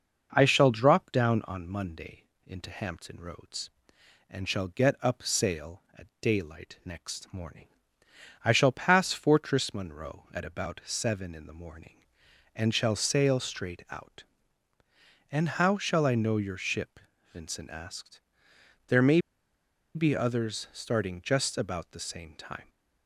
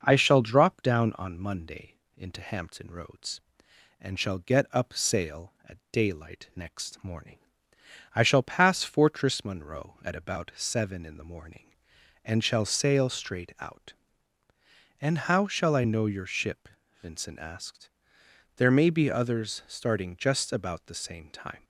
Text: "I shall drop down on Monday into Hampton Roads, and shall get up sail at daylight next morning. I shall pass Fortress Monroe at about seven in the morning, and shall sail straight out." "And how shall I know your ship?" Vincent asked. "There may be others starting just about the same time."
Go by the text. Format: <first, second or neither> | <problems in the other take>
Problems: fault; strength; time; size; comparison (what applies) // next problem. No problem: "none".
second | starts louder than the rest; noticeable; until 1.3 s; 6 dB; noticeable in the second // pauses between "Monday" and "into"; slight; at 2.2 s; 0.24 s long; slight in the second // pauses between "may" and "be"; noticeable; at 19.1 s; 0.76 s long